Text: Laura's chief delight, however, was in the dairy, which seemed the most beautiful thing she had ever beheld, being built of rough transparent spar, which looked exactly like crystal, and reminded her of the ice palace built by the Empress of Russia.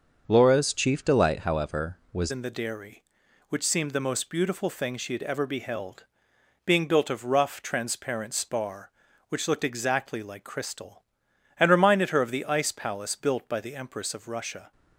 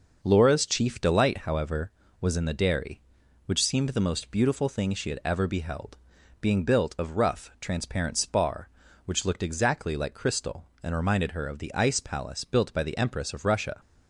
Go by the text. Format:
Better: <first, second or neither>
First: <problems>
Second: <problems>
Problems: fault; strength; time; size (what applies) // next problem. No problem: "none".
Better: second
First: starts louder than the rest; until 1.2 s; 6.5 dB // changes voice at "in"; from 2.2 s on; 12.5 s long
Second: none